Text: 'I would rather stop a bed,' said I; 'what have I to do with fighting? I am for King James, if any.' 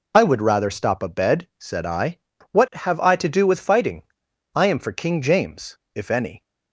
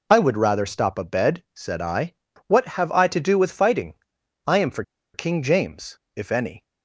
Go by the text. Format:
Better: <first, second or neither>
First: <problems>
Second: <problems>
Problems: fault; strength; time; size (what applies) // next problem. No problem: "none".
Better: first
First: none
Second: pauses between "for" and "King"; slight; at 4.8 s; 0.31 s long